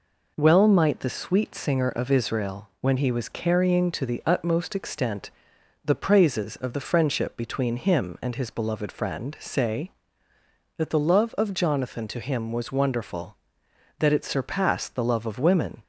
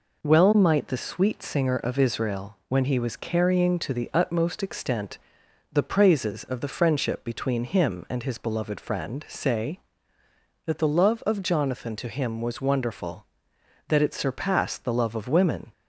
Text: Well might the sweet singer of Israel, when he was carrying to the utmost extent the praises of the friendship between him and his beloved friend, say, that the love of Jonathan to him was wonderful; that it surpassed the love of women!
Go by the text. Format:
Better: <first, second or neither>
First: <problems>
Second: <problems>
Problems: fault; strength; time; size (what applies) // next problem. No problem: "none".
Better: neither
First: pauses between "extent" and "the"; noticeable; at 5.3 s; 0.54 s long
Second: pauses between "extent" and "the"; noticeable; at 5.1 s; 0.54 s long